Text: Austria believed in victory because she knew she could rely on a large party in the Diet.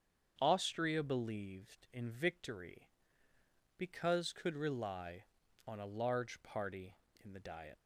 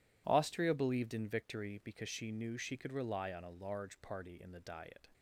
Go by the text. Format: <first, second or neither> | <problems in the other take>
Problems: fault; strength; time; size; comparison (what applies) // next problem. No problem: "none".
second | starts louder than the rest; strong; until 1.4 s; 7.5 dB // skips "she knew she"; at 4.3 s